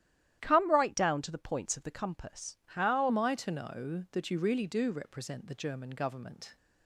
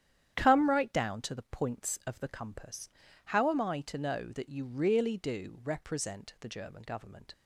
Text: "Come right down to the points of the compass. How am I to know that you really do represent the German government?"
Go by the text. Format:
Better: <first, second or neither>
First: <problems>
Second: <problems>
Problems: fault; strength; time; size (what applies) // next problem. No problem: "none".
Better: second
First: starts louder than the rest; strong; until 1.4 s; 12 dB // changes voice at "am"; from 3.0 s on; 3.5 s long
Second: starts louder than the rest; strong; until 1.3 s; 10 dB